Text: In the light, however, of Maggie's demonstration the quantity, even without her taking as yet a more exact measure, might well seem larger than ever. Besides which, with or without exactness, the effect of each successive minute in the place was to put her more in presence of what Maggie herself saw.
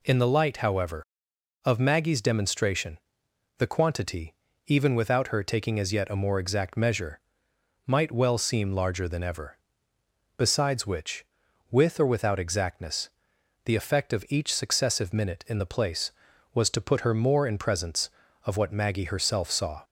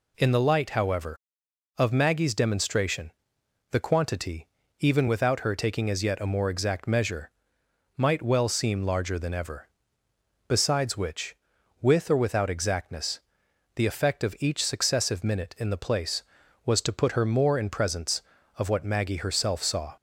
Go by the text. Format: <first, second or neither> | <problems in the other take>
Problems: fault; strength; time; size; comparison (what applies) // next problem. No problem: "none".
neither | pauses between "demonstration" and "the"; noticeable; the same in both